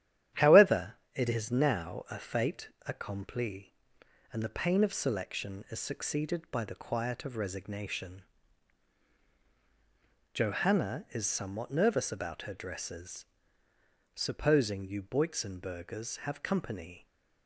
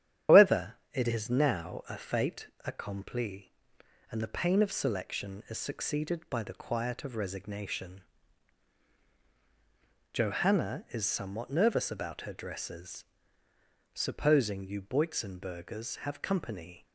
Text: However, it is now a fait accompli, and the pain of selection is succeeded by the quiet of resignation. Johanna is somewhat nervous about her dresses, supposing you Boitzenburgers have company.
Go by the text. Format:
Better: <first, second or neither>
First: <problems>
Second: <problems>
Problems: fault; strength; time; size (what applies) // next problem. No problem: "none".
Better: first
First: starts louder than the rest; strong; until 1.5 s; 11 dB // pauses between "fait" and "accompli"; slight; at 2.6 s; 0.20 s long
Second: loses the start of "However"; at 0.2 s; 155 ms // starts louder than the rest; strong; until 1.4 s; 10.5 dB // pauses between "fait" and "accompli"; slight; at 2.4 s; 0.20 s long